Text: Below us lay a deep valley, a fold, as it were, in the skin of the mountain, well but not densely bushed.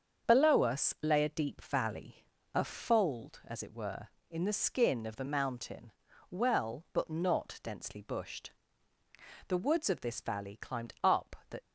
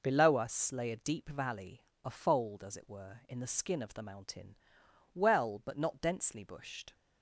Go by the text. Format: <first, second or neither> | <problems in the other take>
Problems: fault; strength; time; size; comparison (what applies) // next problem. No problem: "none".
second | starts louder than the rest; until 1.3 s; 7 dB // goes on to say "The woods of this valley climbed up the"; strong; from 9.4 s on; 2.1 s long